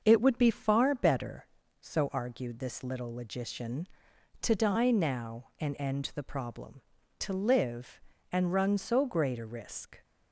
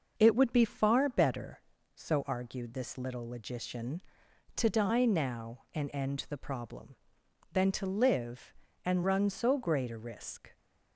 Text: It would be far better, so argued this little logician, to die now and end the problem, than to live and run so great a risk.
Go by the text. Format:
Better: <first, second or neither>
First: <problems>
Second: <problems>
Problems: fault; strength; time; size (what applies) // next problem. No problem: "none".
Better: second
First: starts louder than the rest; noticeable; until 1.0 s; 6 dB // skips "than"; at 7.0 s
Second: none